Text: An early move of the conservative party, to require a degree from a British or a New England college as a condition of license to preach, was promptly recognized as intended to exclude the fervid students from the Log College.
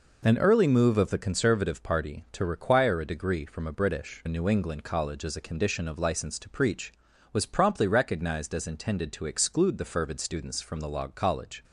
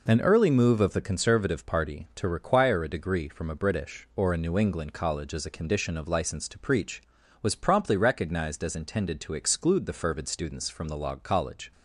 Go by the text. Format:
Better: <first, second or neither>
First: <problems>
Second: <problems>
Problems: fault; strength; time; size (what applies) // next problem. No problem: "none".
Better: second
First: skips "or"; at 4.2 s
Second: none